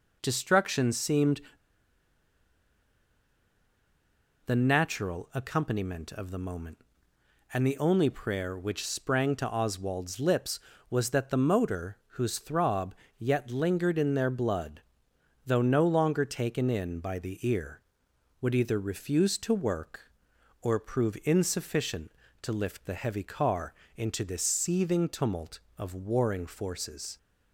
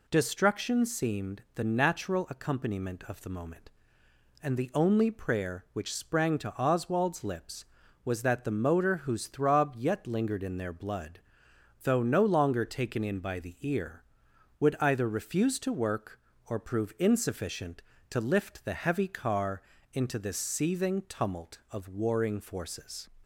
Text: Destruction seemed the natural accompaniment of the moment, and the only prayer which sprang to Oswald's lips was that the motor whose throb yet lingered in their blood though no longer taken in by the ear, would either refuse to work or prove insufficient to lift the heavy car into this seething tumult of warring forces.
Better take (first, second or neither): second